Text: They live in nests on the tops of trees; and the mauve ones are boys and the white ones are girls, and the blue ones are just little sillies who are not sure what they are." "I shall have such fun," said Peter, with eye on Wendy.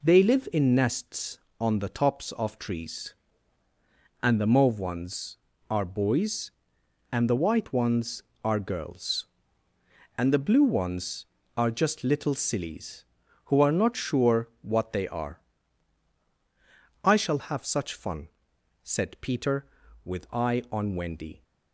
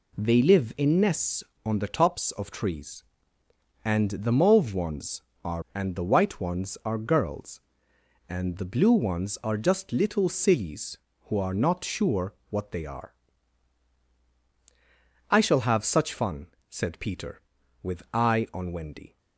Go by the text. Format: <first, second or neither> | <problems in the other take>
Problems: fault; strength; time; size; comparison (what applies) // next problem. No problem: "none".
first | skips "boys"; at 5.6 s // pauses between "sure" and "what"; slight; at 12.3 s; 0.16 s long